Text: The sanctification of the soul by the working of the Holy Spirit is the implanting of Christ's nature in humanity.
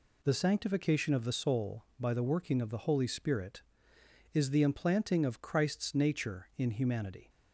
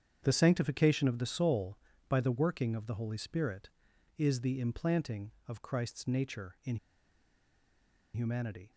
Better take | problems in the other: first | starts louder than the rest; strong; until 1.2 s; 8 dB // pauses between "in" and "humanity"; strong; at 6.7 s; 1.3 s long

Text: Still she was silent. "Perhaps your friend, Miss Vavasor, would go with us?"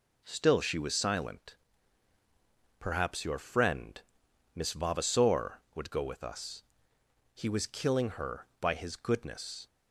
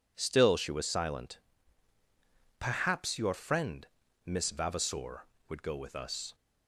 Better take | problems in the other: second | goes on to say "He was killing her by his goodness"; strong; from 7.3 s on; 2.3 s long

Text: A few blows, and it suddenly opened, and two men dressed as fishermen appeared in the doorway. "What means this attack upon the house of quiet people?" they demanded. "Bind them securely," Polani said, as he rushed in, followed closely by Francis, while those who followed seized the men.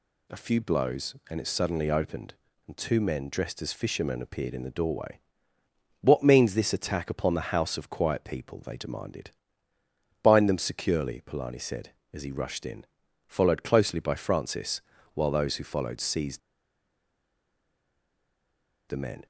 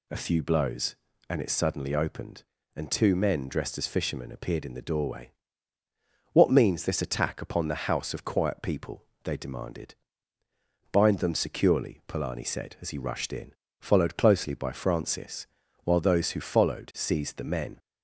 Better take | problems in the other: second | pauses between "seized" and "the"; strong; at 16.3 s; 2.4 s long

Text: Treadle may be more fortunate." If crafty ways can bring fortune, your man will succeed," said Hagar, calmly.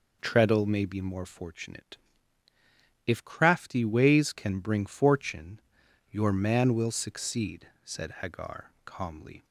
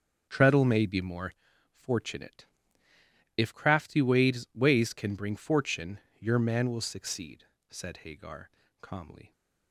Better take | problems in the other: first | starts louder than the rest; until 1.3 s; 7 dB // pauses between "more" and "fortunate"; at 1.3 s; 0.38 s long // says "ways" twice; at 4.5 s

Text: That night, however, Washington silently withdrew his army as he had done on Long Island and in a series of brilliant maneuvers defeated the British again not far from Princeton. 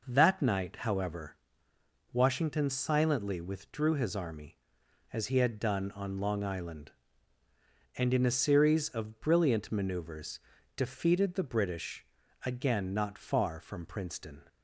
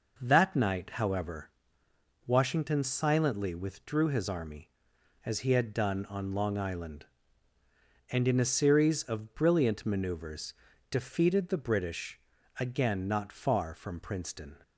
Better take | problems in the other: neither | pauses between "maneuvers" and "defeated"; slight; the same in both // pauses between "British" and "again"; the same in both

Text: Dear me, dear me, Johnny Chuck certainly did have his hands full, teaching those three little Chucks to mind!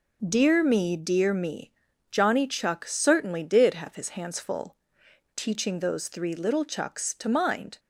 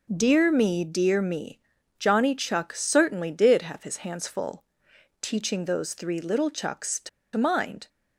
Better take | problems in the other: first | pauses between "to" and "mind"; slight; at 7.0 s; 0.26 s long

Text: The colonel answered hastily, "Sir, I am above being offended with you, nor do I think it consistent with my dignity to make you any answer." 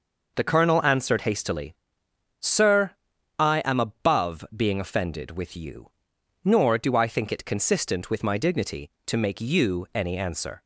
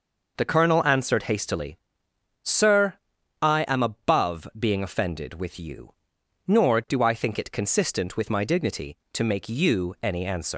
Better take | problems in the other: first | leaves "answer" unfinished; at 10.5 s; 140 ms

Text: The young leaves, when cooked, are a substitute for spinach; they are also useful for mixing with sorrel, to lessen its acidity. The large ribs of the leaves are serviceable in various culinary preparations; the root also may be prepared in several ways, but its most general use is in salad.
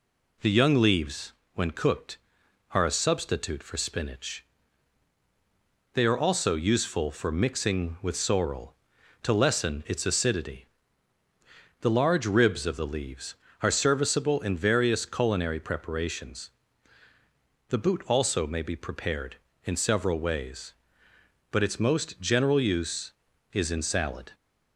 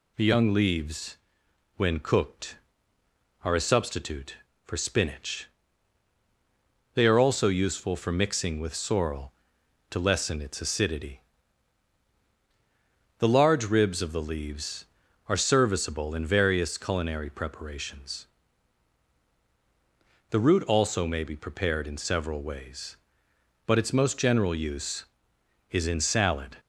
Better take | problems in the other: second | says "boot" for "root"; at 17.7 s

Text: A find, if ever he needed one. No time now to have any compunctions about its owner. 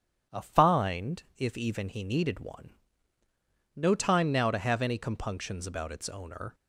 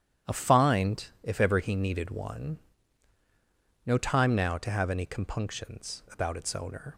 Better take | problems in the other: second | starts louder than the rest; strong; until 1.4 s; 9.5 dB; strong in the second // says "even" for "ever"; at 1.5 s

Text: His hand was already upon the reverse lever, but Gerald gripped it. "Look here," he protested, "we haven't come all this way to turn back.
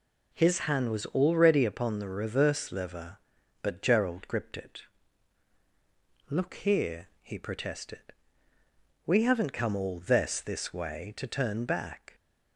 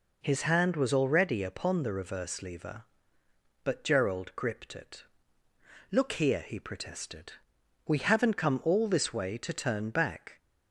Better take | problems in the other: second | says "this" twice; at 10.4 s

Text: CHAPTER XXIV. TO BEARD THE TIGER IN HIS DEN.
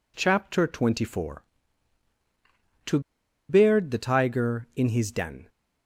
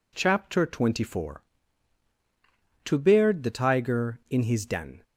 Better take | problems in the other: second | pauses between "TO" and "BEARD"; noticeable; at 2.9 s; 0.49 s long

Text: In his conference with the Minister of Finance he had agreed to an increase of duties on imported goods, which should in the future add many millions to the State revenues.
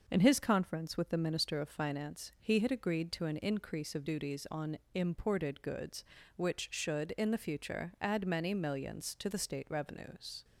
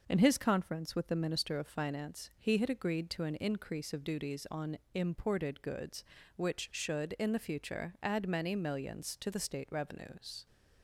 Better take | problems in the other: neither | pauses between "on" and "imported"; slight; the same in both

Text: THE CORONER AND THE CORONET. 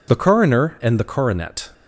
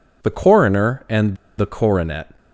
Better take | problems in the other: first | pauses between "AND" and "THE"; slight; at 1.3 s; 0.22 s long

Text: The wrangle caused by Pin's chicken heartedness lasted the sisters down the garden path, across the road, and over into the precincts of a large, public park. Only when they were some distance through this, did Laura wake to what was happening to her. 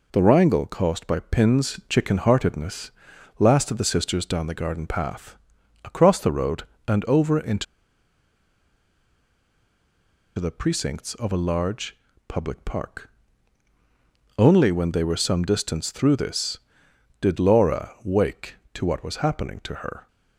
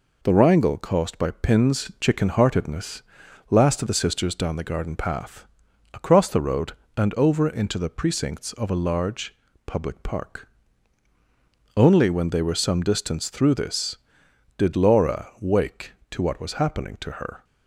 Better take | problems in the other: second | pauses between "heartedness" and "lasted"; noticeable; at 2.8 s; 0.48 s long; noticeable in the second // pauses between "into" and "the"; strong; at 7.6 s; 2.7 s long

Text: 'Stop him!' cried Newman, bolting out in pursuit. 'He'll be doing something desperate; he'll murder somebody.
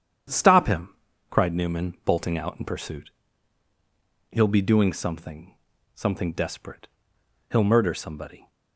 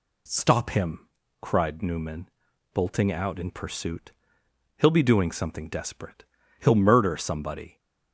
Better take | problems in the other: second | starts louder than the rest; strong; until 1.7 s; 9 dB // says "something" twice; at 5.9 s

